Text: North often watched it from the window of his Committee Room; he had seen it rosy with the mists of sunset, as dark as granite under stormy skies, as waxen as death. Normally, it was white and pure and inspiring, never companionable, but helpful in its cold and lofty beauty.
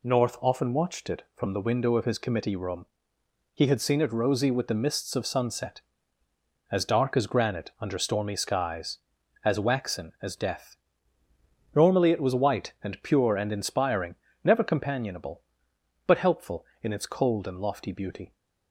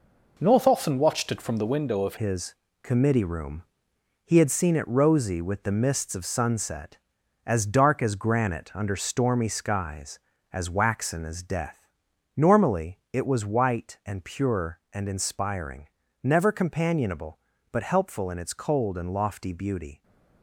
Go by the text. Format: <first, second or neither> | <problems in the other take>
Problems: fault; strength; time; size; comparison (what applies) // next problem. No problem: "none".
first | changes voice at "his"; from 2.1 s on; 17.9 s long // pauses between "his" and "Committee"; slight; at 2.5 s; 0.26 s long